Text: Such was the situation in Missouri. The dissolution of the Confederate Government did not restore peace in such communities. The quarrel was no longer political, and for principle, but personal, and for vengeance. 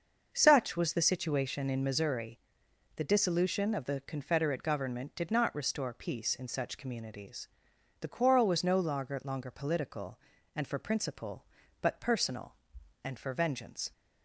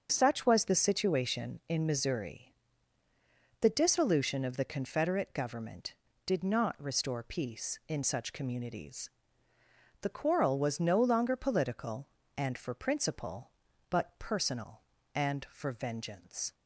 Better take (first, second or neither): second